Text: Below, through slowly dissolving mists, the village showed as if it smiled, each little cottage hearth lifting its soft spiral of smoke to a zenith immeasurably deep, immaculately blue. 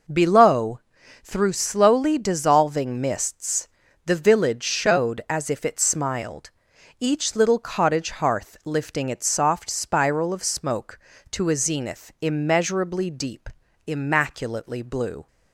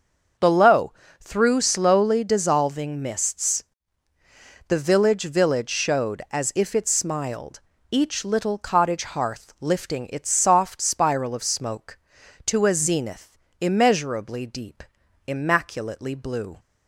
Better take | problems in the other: first | starts louder than the rest; until 1.6 s; 6.5 dB // says "village" twice; at 5.2 s // pauses between "zenith" and "immeasurably"; slight; at 13.3 s; 0.22 s long

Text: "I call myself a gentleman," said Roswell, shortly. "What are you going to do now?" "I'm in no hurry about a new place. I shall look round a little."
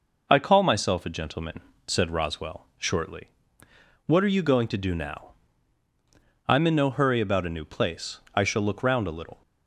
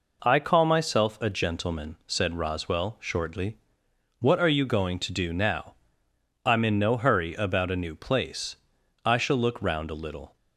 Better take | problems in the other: neither | none

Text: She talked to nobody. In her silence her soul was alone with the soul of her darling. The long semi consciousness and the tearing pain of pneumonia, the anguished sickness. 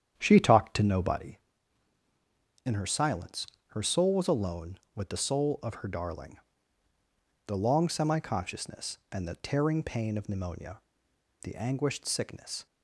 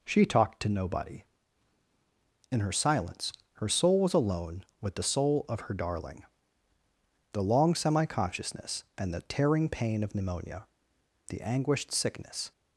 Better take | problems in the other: second | starts louder than the rest; strong; until 1.3 s; 9 dB // pauses between "silence" and "her"; slight; at 3.4 s; 0.22 s long; slight in the second

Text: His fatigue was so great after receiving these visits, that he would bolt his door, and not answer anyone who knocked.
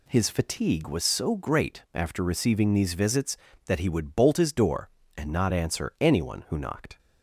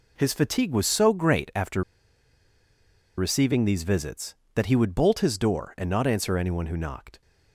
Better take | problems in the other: first | pauses between "after" and "receiving"; strong; at 1.8 s; 1.3 s long

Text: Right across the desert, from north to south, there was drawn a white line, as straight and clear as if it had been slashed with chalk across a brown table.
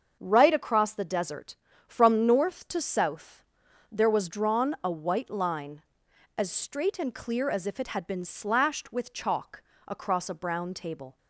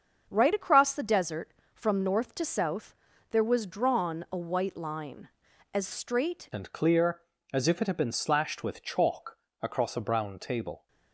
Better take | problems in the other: first | starts louder than the rest; until 1.3 s; 7 dB; also in the first // changes voice at "and"; from 6.5 s on; 4.3 s long // pauses between "chalk" and "across"; slight; at 9.3 s; 0.24 s long; slight in the first

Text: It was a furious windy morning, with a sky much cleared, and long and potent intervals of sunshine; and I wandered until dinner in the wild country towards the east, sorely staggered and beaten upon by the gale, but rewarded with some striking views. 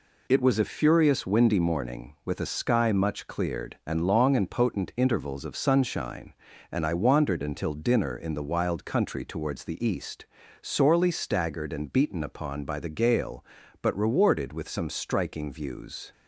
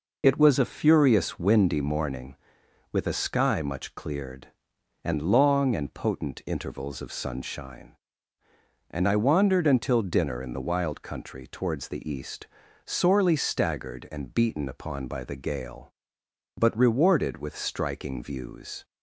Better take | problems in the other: first | skips "some"; at 17.5 s

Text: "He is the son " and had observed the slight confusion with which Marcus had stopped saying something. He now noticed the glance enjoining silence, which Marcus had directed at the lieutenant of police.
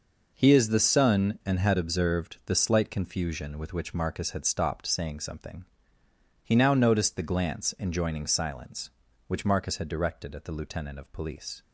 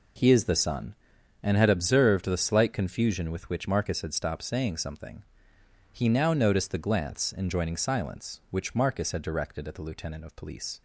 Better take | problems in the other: neither | none

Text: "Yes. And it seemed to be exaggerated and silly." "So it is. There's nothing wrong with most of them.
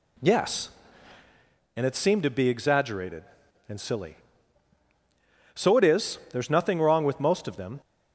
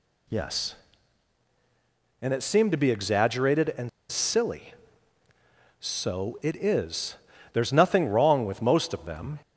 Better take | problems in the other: first | pauses between "and" and "silly"; slight; at 3.8 s; 0.20 s long

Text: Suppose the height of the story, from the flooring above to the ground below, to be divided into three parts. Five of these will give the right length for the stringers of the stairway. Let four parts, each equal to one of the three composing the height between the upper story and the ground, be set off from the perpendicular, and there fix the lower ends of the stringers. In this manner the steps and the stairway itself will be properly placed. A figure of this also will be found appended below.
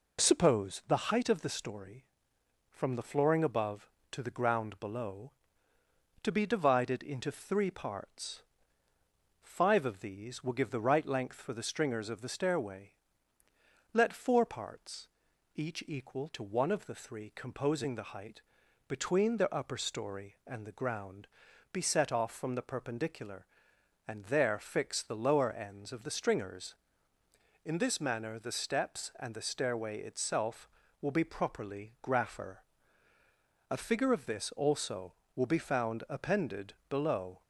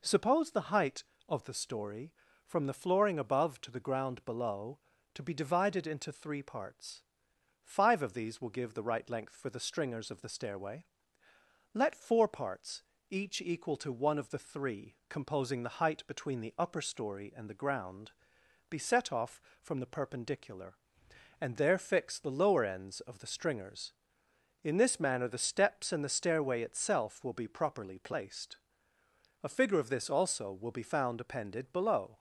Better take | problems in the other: second | pauses between "height" and "between"; noticeable; at 18.4 s; 0.48 s long // says "grapher" for "placed"; at 32.0 s // pauses between "appended" and "below"; slight; at 36.7 s; 0.16 s long

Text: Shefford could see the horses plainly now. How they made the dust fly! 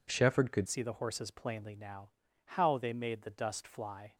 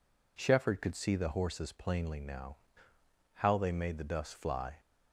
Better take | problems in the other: second | changes voice at "see"; from 0.6 s on; 3.5 s long

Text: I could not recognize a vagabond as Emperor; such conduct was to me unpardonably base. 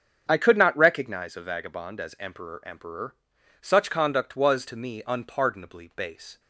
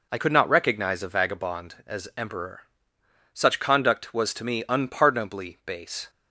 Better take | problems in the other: second | starts louder than the rest; strong; until 1.3 s; 7.5 dB // says "Emperor" twice; at 2.6 s

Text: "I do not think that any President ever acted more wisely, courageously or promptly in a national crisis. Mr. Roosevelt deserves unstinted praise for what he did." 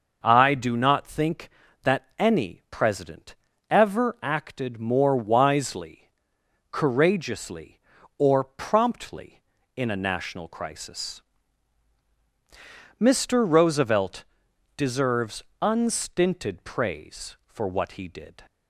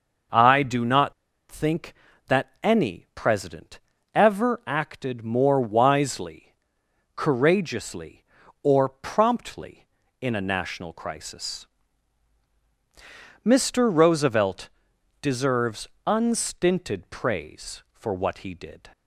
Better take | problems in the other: first | starts louder than the rest; noticeable; until 1.6 s; 6 dB // pauses between "not" and "think"; at 1.1 s; 0.37 s long // pauses between "President" and "ever"; slight; at 3.7 s; 0.34 s long; slight in the first // pauses between "Roosevelt" and "deserves"; noticeable; at 14.6 s; 0.52 s long; noticeable in the first // pauses between "deserves" and "unstinted"; slight; at 15.8 s; 0.18 s long; slight in the first

